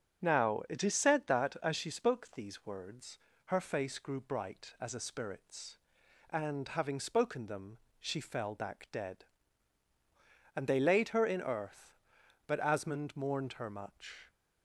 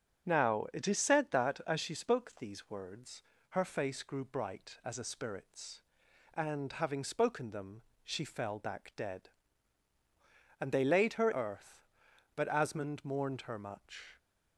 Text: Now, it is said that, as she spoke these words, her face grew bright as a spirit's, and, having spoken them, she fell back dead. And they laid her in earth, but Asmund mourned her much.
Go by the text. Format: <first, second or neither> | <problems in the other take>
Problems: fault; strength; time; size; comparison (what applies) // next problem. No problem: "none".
first | starts louder than the rest; strong; until 1.3 s; 8.5 dB; strong in the first // skips "in"; at 11.3 s